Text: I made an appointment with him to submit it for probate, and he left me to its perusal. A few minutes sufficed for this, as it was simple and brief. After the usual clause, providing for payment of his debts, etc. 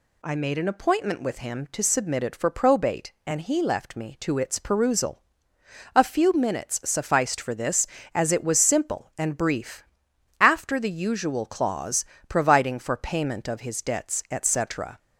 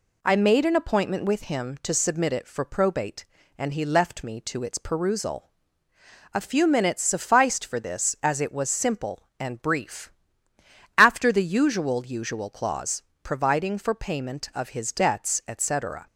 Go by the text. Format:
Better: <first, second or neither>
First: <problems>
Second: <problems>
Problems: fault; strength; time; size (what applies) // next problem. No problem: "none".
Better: first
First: none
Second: says "usual" twice; at 12.0 s